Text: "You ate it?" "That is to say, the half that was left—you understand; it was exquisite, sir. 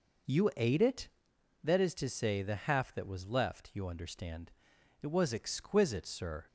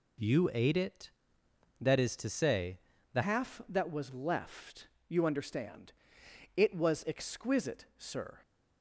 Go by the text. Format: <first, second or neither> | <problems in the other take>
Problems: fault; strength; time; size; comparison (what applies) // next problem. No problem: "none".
first | changes voice at "half"; from 3.2 s on; 5.2 s long